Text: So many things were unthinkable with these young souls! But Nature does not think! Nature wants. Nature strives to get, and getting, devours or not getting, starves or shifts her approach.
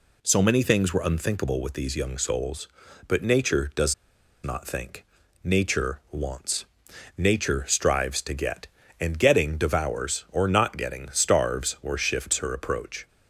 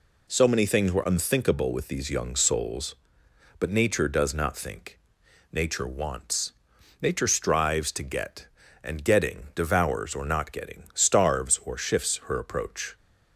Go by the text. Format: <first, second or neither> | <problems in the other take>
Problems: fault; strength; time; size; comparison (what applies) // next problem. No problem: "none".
second | pauses between "does" and "not"; noticeable; at 3.9 s; 0.50 s long